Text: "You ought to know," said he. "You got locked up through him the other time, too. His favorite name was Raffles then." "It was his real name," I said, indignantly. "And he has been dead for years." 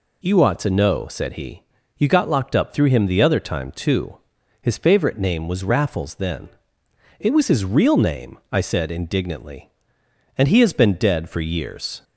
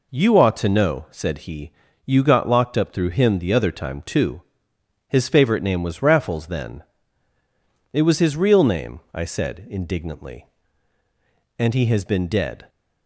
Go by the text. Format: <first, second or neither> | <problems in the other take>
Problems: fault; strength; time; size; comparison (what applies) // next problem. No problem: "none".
first | stops before "for years"; at 12.6 s